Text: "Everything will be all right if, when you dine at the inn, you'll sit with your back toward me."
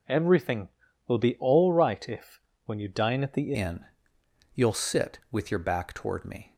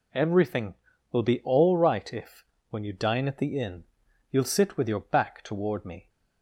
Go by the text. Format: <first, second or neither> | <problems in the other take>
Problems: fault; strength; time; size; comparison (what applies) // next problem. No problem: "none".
second | changes voice at "inn"; from 3.5 s on; 3.0 s long